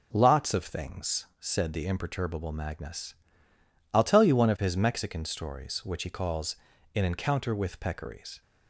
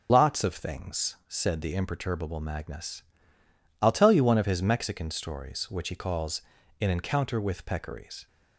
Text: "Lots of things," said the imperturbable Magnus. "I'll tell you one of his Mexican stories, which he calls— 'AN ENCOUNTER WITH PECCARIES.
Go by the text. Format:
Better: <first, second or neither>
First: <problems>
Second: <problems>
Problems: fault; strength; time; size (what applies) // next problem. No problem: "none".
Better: first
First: none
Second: loses the start of "Lots"; at 0.0 s; 85 ms